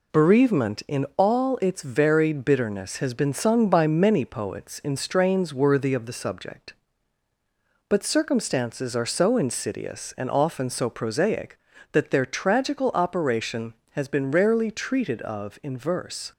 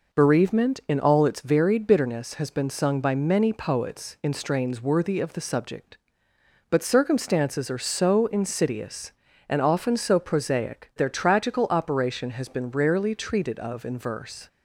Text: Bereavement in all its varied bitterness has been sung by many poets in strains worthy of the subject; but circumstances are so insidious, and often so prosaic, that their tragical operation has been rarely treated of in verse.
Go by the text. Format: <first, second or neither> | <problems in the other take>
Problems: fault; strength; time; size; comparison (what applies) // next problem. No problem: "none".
first | skips "that"; at 10.9 s